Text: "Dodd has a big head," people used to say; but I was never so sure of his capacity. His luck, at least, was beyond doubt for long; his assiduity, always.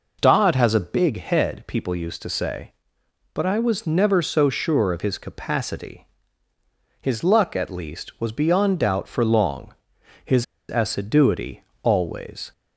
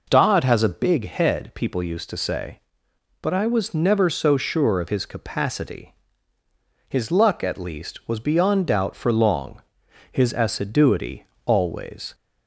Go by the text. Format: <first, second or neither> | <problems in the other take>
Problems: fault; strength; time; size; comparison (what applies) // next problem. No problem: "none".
second | pauses between "his" and "assiduity"; slight; at 10.4 s; 0.24 s long